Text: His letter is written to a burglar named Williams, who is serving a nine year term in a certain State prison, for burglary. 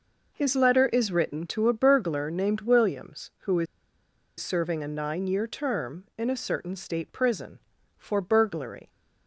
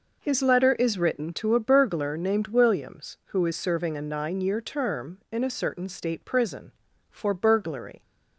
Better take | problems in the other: second | pauses between "is" and "serving"; noticeable; at 3.6 s; 0.74 s long

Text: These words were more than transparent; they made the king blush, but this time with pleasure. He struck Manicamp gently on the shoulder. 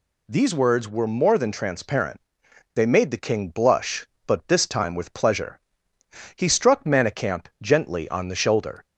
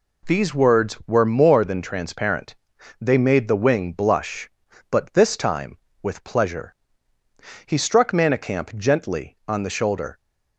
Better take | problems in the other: first | says "wing" for "king"; at 3.5 s

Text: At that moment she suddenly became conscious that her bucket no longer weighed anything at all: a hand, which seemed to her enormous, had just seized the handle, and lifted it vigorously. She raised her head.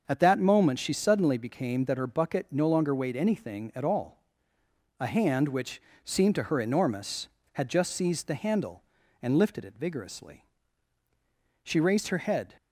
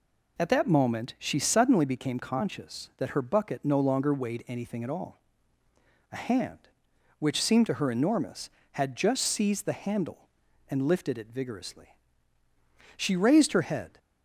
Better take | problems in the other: second | starts louder than the rest; until 1.0 s; 6.5 dB // skips "conscious"; at 1.8 s // pauses between "which" and "seemed"; slight; at 5.8 s; 0.22 s long

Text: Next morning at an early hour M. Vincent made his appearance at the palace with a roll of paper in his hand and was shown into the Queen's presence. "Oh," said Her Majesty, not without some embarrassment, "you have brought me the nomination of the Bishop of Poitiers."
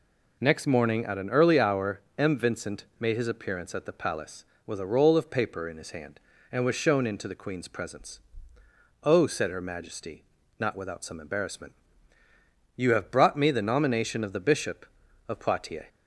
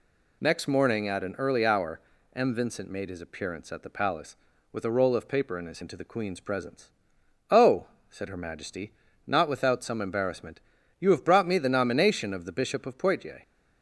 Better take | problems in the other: first | pauses between "hour" and "M"; slight; at 2.0 s; 0.34 s long // skips "hand and was shown"; at 5.8 s

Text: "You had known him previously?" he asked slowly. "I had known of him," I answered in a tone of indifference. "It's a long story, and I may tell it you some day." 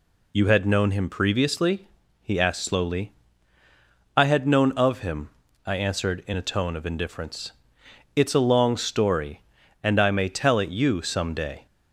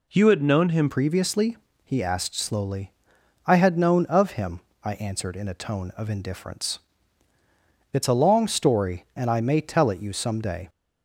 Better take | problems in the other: first | changes voice at "previously"; from 0.8 s on; 9.8 s long

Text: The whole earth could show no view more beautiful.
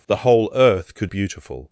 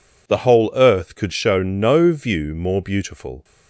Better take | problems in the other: second | skips "show no view more"; at 1.0 s

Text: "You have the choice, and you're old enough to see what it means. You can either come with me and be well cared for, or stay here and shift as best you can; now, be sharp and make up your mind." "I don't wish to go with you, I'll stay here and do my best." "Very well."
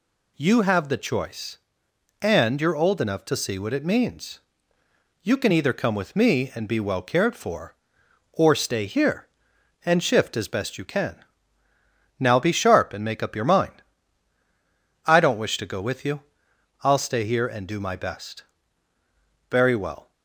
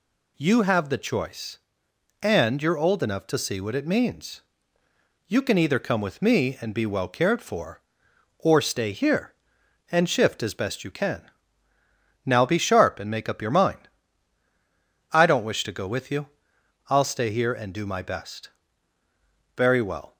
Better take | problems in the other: neither | none

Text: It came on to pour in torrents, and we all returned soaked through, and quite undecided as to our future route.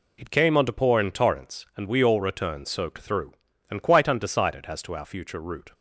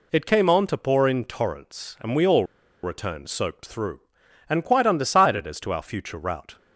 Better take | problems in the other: first | pauses between "all" and "returned"; at 2.4 s; 0.39 s long

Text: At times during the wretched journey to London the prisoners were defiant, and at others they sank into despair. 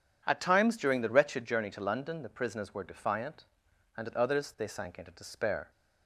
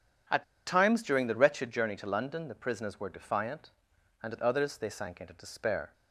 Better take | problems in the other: first | pauses between "At" and "times"; slight; at 0.4 s; 0.23 s long

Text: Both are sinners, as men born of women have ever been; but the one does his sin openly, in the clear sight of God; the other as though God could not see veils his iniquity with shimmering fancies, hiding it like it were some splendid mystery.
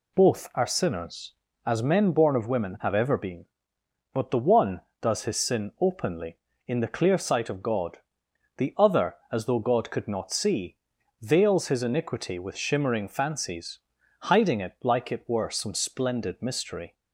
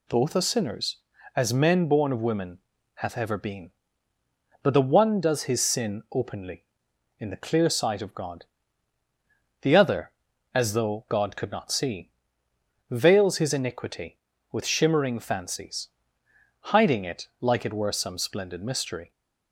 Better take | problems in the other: first | says "hath" for "have"; at 2.9 s // pauses between "see" and "veils"; noticeable; at 12.1 s; 0.80 s long; noticeable in the first

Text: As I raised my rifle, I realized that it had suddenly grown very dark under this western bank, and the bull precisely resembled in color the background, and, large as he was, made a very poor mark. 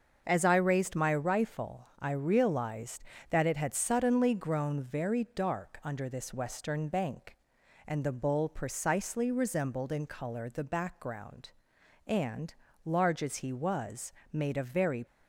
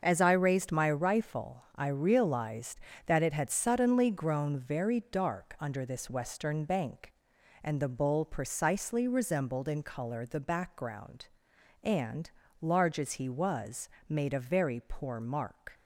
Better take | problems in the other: second | starts louder than the rest; until 1.2 s; 6.5 dB; also in the second // stops before "poor mark"; at 15.0 s

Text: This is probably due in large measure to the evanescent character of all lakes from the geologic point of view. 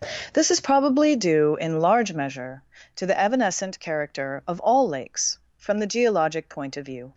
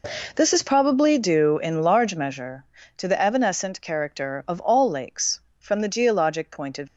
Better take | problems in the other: first | stops before "view"; at 6.8 s

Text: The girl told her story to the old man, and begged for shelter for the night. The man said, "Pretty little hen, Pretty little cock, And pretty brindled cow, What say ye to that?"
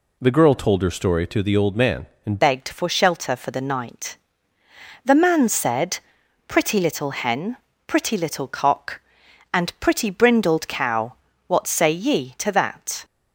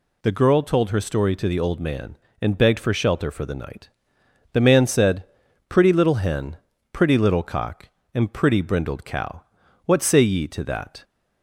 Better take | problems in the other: second | changes voice at "begged"; from 2.4 s on; 10.6 s long

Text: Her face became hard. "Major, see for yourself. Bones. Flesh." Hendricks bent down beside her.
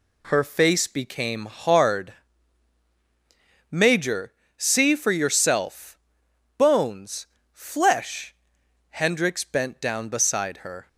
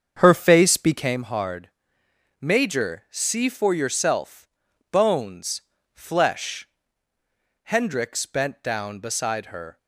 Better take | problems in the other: first | starts louder than the rest; strong; until 1.2 s; 7 dB

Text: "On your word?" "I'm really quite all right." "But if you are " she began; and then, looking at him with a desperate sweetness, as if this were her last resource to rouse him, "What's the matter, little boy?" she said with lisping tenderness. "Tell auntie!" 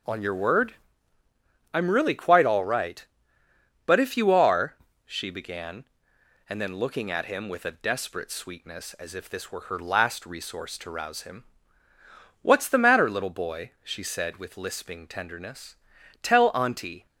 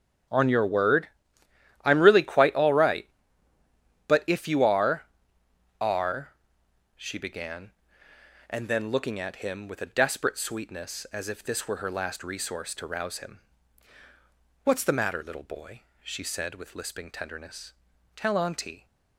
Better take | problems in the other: first | starts louder than the rest; strong; until 2.0 s; 9.5 dB // says "are" twice; at 5.7 s

